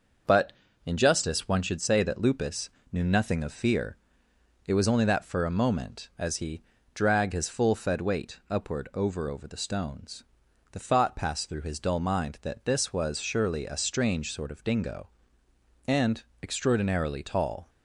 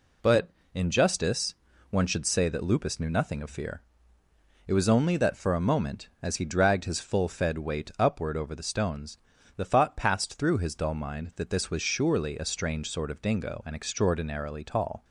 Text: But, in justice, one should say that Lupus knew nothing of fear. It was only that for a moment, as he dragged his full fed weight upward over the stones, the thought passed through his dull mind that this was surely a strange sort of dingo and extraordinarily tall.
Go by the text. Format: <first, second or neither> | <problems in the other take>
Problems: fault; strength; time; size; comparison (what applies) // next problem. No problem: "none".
second | starts louder than the rest; noticeable; until 1.5 s; 6 dB // pauses between "Lupus" and "knew"; slight; at 2.6 s; 0.24 s long // pauses between "he" and "dragged"; slight; at 6.6 s; 0.30 s long // says "over" twice; at 9.2 s // pauses between "and" and "extraordinarily"; slight; at 16.2 s; 0.18 s long